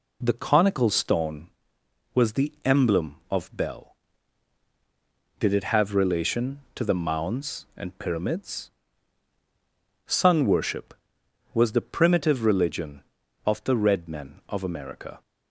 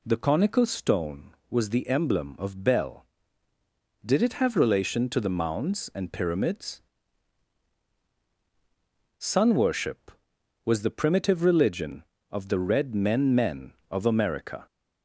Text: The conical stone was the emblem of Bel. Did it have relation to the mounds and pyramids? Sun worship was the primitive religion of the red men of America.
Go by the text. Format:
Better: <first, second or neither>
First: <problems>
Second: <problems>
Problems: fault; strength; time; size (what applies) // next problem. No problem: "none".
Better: first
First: none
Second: says "men" twice; at 13.3 s